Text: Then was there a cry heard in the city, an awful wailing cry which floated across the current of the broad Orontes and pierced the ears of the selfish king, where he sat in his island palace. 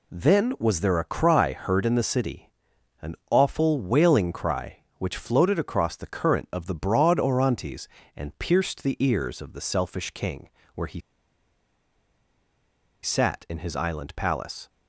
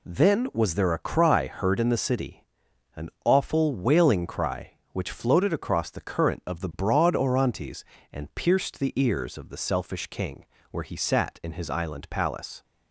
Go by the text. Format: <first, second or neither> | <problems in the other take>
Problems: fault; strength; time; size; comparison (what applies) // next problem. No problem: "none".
second | pauses between "an" and "awful"; slight; at 3.1 s; 0.16 s long; slight in the second // pauses between "he" and "sat"; strong; at 10.9 s; 2.0 s long